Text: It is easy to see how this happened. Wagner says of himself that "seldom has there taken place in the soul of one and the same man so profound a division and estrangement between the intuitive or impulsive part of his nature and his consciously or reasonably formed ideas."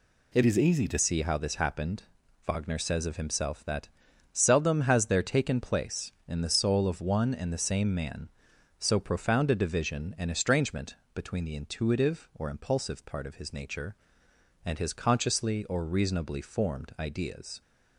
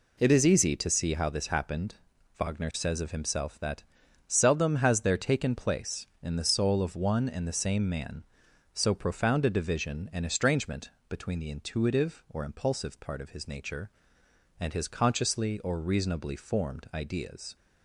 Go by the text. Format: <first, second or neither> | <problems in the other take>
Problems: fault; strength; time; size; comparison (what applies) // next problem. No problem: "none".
second | changes voice from "is" to "to"; from 0.4 to 0.9 s; 0.5 s long // pauses between "that" and "seldom"; noticeable; at 3.8 s; 0.46 s long; noticeable in the second // pauses between "estrangement" and "between"; slight; at 10.9 s; 0.18 s long; slight in the second